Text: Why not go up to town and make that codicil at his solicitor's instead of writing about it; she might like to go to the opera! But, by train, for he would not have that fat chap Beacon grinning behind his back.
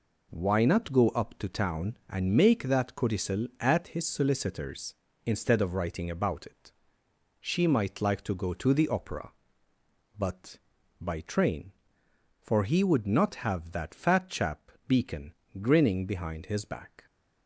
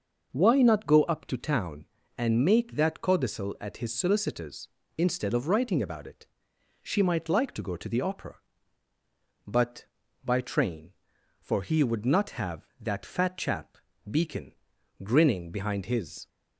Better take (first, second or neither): first